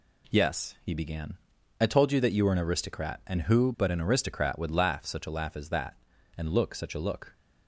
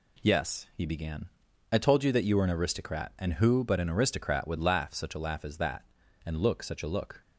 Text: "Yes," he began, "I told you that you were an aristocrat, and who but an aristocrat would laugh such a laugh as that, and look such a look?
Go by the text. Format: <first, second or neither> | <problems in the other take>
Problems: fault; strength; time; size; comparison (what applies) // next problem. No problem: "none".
neither | none